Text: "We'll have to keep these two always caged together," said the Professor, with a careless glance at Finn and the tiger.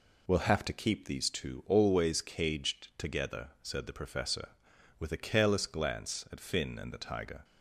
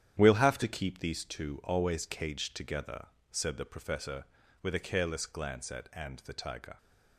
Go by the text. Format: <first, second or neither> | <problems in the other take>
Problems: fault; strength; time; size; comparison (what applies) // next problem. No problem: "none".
first | starts louder than the rest; strong; until 1.1 s; 10 dB // skips "Finn"; at 5.9 s